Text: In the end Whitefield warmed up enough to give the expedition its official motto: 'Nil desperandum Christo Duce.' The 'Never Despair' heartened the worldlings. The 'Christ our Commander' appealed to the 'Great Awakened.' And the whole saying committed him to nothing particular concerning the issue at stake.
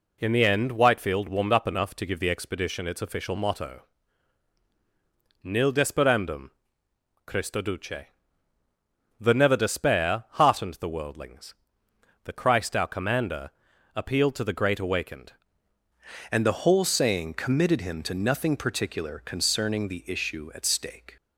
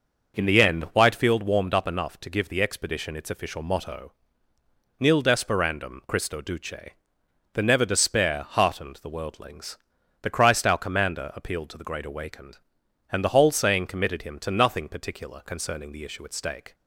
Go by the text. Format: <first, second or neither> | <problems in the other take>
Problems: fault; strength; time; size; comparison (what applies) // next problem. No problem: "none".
second | pauses between "desperandum" and "Christo"; noticeable; at 6.5 s; 0.74 s long // pauses between "Commander" and "appealed"; at 13.5 s; 0.44 s long // changes voice at "And"; from 16.3 s on; 4.8 s long